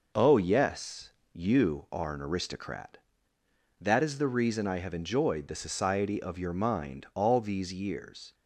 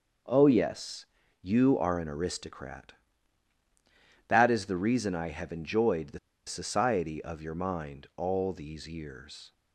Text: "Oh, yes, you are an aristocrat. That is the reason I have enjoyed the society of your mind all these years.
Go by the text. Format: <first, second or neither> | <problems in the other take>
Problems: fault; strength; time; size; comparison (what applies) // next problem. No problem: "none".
first | pauses between "the" and "society"; slight; at 6.1 s; 0.28 s long